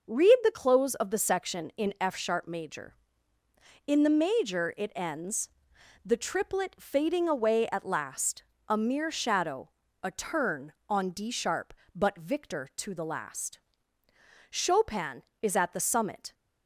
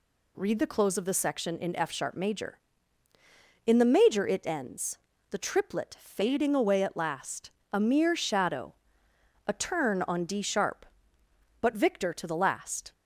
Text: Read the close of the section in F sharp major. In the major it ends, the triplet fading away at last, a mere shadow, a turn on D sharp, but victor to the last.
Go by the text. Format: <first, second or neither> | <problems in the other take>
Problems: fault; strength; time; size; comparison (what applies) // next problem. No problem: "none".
second | goes on to say "Chopin is at the summit"; strong; from 14.4 s on; 1.8 s long